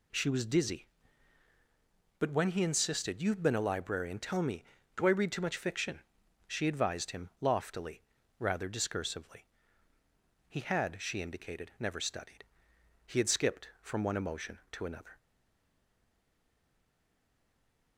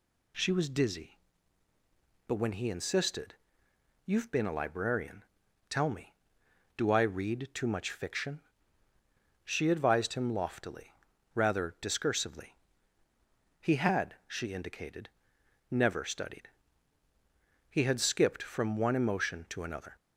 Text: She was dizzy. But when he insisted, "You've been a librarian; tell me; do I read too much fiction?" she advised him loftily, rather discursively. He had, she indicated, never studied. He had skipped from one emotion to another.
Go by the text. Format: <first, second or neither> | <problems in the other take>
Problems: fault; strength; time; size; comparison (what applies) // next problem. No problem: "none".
second | stays silent after the last word; strong; from 15.1 s on; 2.8 s long